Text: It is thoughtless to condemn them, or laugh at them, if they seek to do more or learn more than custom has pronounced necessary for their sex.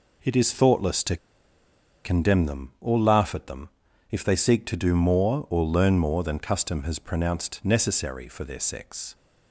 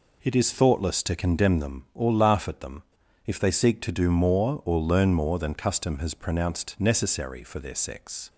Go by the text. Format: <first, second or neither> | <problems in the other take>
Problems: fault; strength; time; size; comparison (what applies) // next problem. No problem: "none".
second | pauses between "to" and "condemn"; noticeable; at 1.1 s; 0.87 s long